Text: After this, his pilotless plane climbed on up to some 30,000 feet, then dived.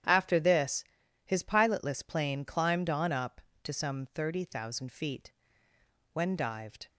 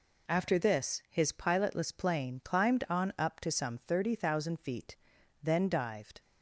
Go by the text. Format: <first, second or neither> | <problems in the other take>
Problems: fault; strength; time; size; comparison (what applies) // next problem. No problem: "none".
second | starts louder than the rest; strong; until 1.4 s; 10 dB // says "when" for "then"; at 6.1 s